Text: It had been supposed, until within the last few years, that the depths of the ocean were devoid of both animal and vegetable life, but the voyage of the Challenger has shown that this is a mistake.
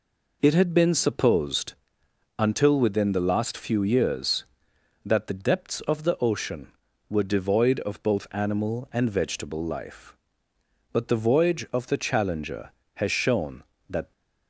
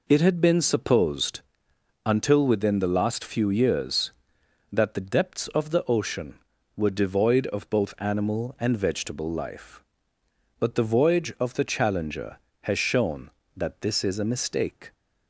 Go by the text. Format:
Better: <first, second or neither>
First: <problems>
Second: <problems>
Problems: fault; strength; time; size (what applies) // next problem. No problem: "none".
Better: second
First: stops before "this is a mistake"; at 14.1 s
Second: none